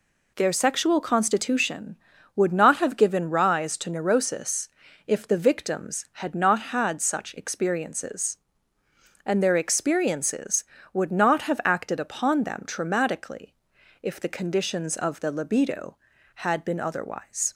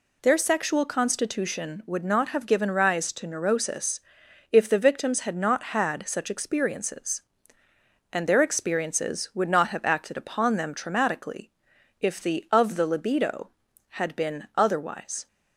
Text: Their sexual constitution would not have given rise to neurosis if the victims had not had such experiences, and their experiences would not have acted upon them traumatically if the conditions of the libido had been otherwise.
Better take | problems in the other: first | pauses between "neurosis" and "if"; noticeable; at 3.9 s; 0.52 s long; also in the first // pauses between "traumatically" and "if"; noticeable; at 11.5 s; 0.50 s long; noticeable in the first // skips "conditions"; at 12.4 s

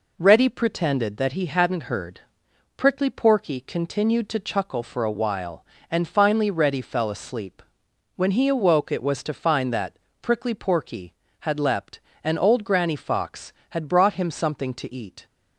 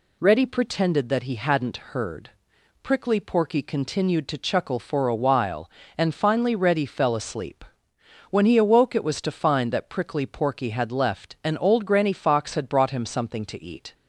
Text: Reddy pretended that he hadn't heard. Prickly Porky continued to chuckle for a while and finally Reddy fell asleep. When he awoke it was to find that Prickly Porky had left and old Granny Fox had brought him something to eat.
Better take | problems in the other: second | pauses between "that" and "Prickly"; slight; at 9.9 s; 0.24 s long // says "leapt" for "left"; at 11.5 s

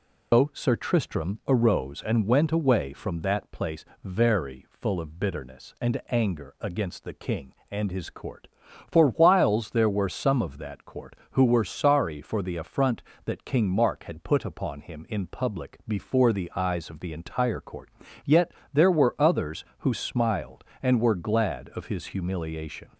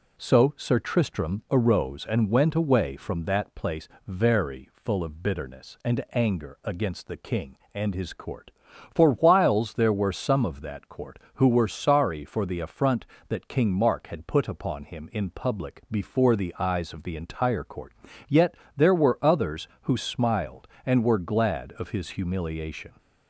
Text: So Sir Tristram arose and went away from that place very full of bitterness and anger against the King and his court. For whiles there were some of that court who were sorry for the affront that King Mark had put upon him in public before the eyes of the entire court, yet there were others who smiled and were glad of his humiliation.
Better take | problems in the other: second | loses the start of "So"; at 0.3 s; 170 ms // pauses between "place" and "very"; slight; at 3.8 s; 0.20 s long; slight in the second // pauses between "yet" and "there"; slight; at 18.5 s; 0.20 s long; slight in the second

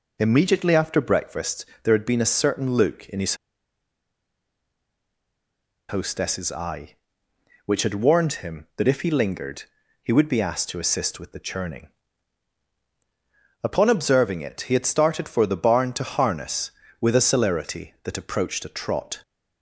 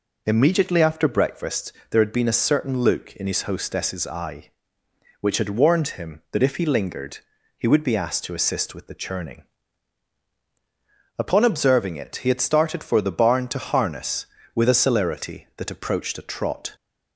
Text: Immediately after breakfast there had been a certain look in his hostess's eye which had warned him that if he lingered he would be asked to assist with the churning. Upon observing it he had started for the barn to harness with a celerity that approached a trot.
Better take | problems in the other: second | pauses between "breakfast" and "there"; slight; at 1.6 s; 0.16 s long; slight in the second // pauses between "his" and "hostess's"; strong; at 3.3 s; 2.5 s long // pauses between "lingered" and "he"; at 9.6 s; 0.38 s long; also in the second

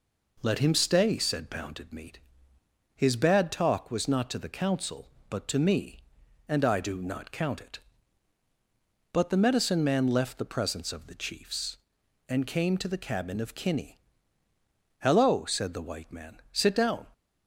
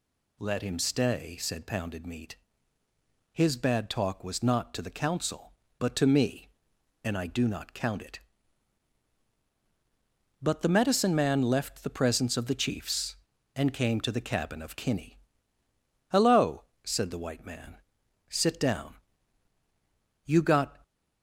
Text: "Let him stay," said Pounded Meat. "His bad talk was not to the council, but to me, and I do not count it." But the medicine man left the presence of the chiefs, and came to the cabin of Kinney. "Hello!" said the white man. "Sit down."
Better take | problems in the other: first | goes on to say "You got"; from 20.2 s on; 0.54 s long

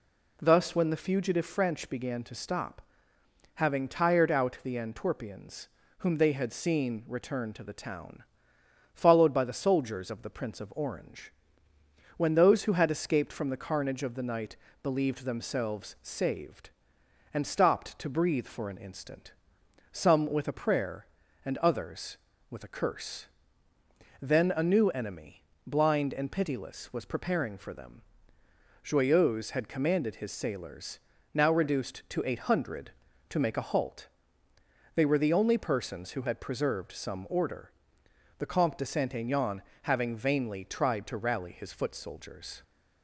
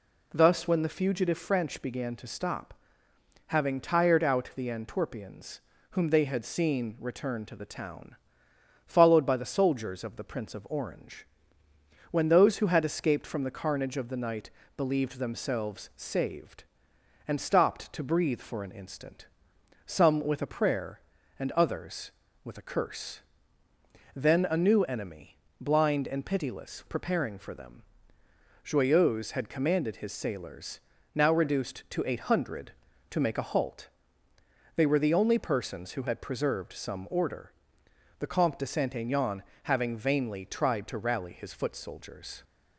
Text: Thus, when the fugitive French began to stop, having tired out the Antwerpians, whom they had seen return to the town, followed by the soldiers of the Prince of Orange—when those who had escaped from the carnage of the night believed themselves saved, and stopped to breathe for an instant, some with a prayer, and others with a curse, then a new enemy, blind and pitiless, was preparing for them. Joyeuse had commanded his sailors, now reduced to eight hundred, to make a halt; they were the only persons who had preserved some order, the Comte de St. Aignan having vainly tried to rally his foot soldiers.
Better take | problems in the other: first | pauses between "night" and "believed"; slight; at 14.5 s; 0.26 s long; slight in the first // skips "was"; at 26.8 s // pauses between "Aignan" and "having"; slight; at 39.4 s; 0.20 s long; slight in the first

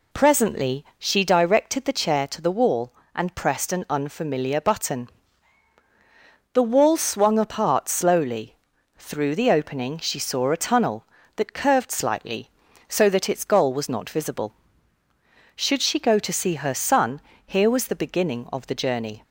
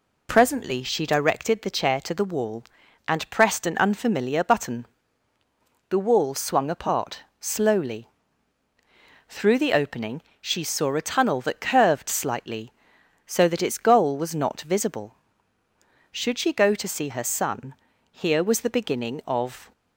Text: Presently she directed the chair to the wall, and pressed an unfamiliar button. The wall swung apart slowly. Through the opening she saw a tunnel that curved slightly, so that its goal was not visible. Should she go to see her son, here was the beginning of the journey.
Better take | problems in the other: first | pauses between "apart" and "slowly"; slight; at 7.2 s; 0.16 s long // pauses between "opening" and "she"; slight; at 10.2 s; 0.18 s long // stops before "the journey"; at 19.7 s

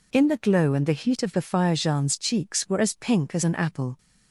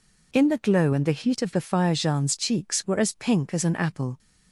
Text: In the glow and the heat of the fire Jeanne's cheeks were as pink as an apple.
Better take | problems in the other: neither | none

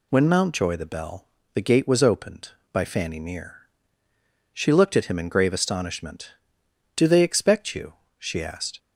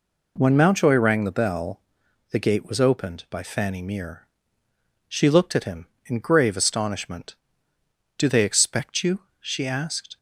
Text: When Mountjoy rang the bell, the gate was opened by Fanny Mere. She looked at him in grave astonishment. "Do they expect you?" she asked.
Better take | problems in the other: second | skips "rang"; at 0.7 s

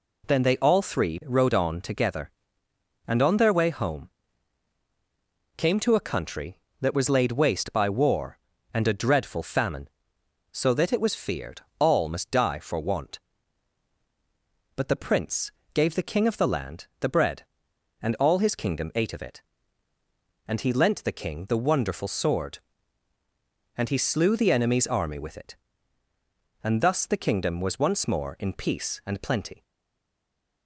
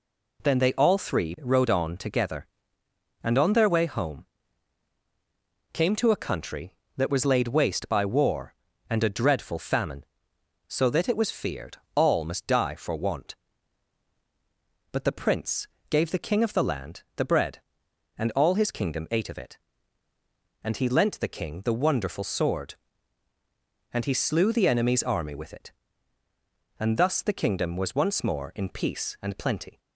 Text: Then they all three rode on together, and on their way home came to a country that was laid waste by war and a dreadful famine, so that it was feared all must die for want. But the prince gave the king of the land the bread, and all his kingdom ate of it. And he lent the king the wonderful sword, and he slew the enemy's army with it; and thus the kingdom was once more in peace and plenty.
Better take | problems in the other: second | pauses between "home" and "came"; strong; at 4.0 s; 1.4 s long; strong in the second // pauses between "feared" and "all"; slight; at 11.6 s; 0.18 s long; slight in the second // pauses between "prince" and "gave"; slight; at 15.5 s; 0.22 s long; slight in the second // stays silent after the last word; from 29.6 s on; 1.0 s long

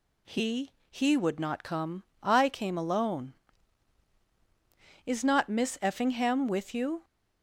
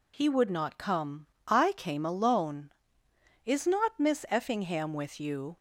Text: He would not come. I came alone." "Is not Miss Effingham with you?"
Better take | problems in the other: second | says "He" twice; at 0.8 s

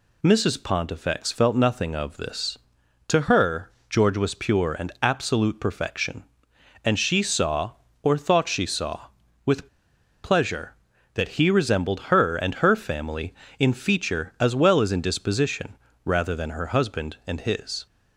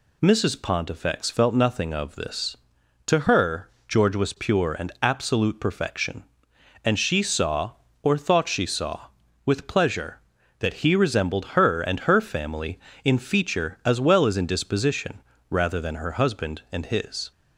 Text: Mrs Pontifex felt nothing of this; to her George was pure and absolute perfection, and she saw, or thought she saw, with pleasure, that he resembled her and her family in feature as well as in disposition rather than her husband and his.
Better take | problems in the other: second | pauses between "her" and "George"; slight; at 3.7 s; 0.18 s long; slight in the second // pauses between "with" and "pleasure"; noticeable; at 9.6 s; 0.57 s long // pauses between "disposition" and "rather"; slight; at 15.7 s; 0.28 s long; slight in the second

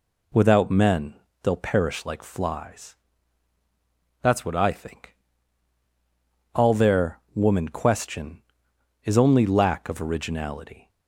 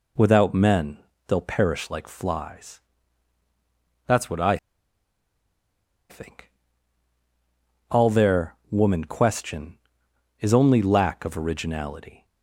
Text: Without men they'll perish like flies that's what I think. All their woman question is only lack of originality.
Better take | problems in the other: first | pauses between "men" and "they'll"; slight; at 0.9 s; 0.30 s long; slight in the first // pauses between "flies" and "that's"; strong; at 2.8 s; 1.2 s long; strong in the first // pauses between "I" and "think"; strong; at 4.5 s; 1.5 s long // pauses between "their" and "woman"; slight; at 8.5 s; 0.16 s long; slight in the first

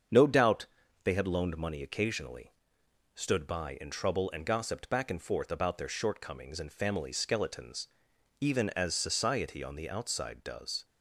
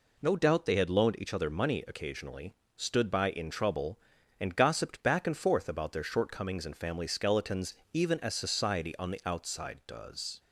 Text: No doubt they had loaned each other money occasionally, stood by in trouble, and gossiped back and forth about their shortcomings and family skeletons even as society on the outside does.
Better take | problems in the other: second | starts louder than the rest; strong; until 1.4 s; 7 dB // pauses between "doubt" and "they"; at 0.6 s; 0.38 s long // skips "each other"; at 1.5 s // pauses between "skeletons" and "even"; noticeable; at 7.8 s; 0.52 s long; slight in the second

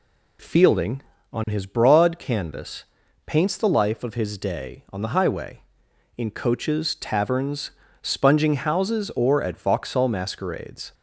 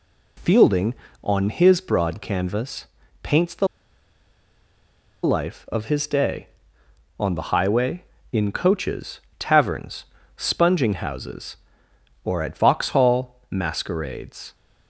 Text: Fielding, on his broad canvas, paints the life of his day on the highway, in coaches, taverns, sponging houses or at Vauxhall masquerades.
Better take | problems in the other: first | pauses between "the" and "life"; strong; at 3.6 s; 1.5 s long

